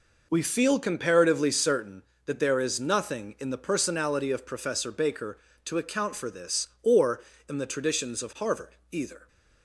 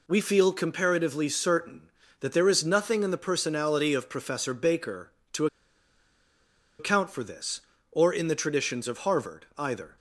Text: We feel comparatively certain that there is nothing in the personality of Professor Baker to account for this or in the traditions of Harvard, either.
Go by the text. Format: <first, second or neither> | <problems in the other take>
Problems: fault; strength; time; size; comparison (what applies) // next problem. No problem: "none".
first | pauses between "to" and "account"; strong; at 5.4 s; 1.3 s long